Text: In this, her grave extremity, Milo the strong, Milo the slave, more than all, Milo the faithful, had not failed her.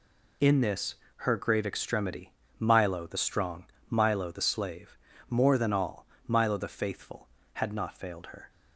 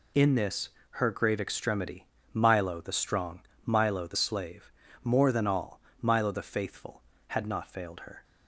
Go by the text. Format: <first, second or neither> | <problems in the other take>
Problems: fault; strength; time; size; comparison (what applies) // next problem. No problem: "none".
neither | none